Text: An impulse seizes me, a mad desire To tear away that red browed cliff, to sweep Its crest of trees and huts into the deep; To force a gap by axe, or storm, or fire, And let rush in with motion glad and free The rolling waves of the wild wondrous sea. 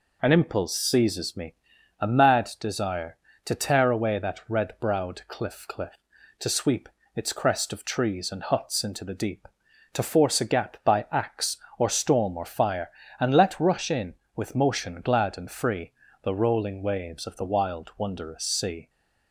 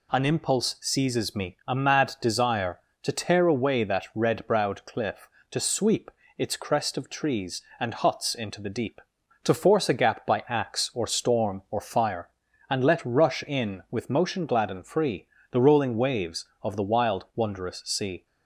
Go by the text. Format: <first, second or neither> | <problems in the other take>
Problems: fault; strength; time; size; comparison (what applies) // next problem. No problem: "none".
second | says "cliff" twice; at 5.6 s // pauses between "sweep" and "Its"; slight; at 6.8 s; 0.26 s long; slight in the second // pauses between "free" and "The"; slight; at 15.9 s; 0.32 s long; slight in the second